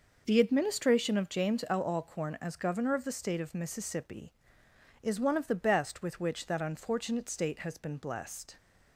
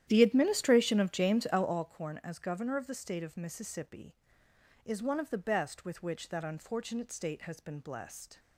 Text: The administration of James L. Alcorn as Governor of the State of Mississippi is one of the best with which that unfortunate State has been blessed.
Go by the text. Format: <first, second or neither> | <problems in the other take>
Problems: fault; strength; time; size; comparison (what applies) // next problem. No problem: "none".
first | starts louder than the rest; strong; until 1.9 s; 11 dB